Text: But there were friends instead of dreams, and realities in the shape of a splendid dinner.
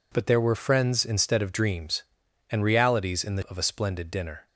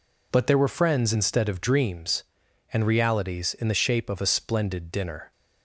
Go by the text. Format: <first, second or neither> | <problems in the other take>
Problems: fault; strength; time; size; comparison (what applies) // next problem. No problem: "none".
second | skips "shape"; at 3.4 s